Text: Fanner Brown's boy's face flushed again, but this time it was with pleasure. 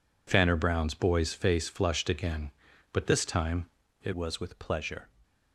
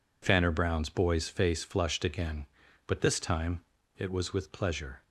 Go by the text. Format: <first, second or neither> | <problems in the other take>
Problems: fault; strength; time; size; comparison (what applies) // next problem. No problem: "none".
second | pauses between "time" and "it"; at 3.6 s; 0.38 s long; also in the second // changes voice at "was"; from 4.1 s on; 1.0 s long